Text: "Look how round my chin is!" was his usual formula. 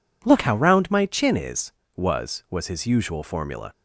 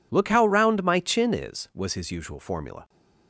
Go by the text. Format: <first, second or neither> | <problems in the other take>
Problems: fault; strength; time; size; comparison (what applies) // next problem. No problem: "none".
second | says "was" twice; at 2.4 s